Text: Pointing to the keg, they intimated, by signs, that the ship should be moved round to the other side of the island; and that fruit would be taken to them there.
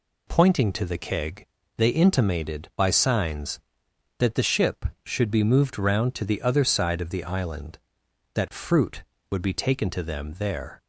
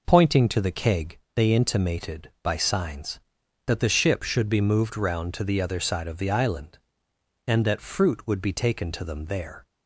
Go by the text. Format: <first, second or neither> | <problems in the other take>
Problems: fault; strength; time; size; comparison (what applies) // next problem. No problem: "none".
second | skips "and"; at 8.0 s